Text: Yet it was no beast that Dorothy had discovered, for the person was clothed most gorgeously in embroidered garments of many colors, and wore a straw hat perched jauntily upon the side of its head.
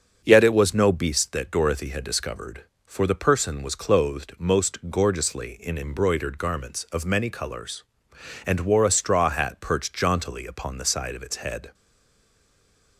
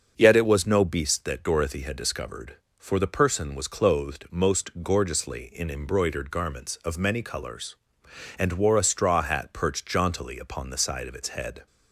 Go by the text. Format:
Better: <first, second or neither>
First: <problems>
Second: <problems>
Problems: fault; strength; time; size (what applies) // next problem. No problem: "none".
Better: second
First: starts louder than the rest; until 1.2 s; 6.5 dB // stays silent after the last word; noticeable; from 11.7 s on; 1.2 s long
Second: starts louder than the rest; until 1.1 s; 6.5 dB